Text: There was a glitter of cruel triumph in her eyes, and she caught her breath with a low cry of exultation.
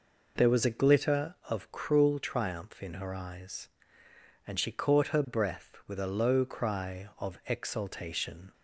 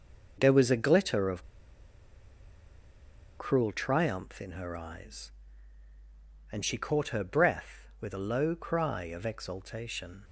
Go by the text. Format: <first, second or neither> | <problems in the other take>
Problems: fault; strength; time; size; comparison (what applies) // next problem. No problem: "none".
first | pauses between "of" and "cruel"; strong; at 1.4 s; 1.9 s long